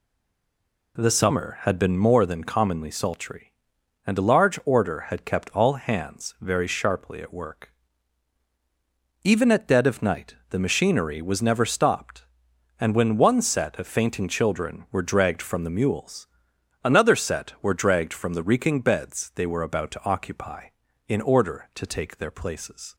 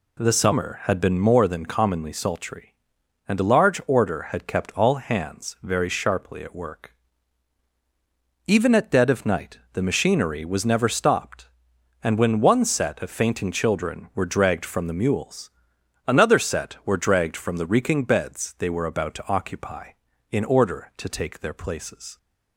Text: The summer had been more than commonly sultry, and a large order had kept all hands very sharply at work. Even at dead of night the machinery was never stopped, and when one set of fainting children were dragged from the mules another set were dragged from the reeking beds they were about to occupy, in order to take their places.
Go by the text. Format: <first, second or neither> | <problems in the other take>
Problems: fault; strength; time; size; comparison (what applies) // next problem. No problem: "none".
second | stays silent before the first word; slight; until 0.9 s; 0.9 s long // pauses between "night" and "the"; slight; at 10.3 s; 0.16 s long; slight in the second // pauses between "mules" and "another"; noticeable; at 16.2 s; 0.58 s long; noticeable in the second